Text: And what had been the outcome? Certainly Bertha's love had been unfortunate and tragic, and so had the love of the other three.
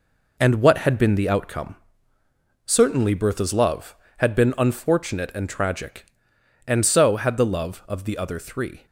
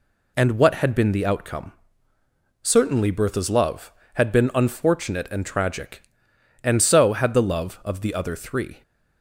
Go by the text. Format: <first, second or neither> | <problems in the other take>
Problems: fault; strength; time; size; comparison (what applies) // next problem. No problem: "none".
second | gets quieter; strong; throughout; 8 dB